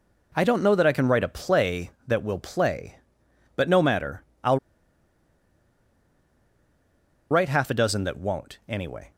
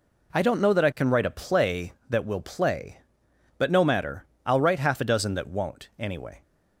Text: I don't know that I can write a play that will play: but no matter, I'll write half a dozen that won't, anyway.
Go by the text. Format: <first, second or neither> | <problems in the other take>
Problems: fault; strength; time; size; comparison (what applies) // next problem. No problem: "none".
second | pauses between "I'll" and "write"; strong; at 4.5 s; 2.7 s long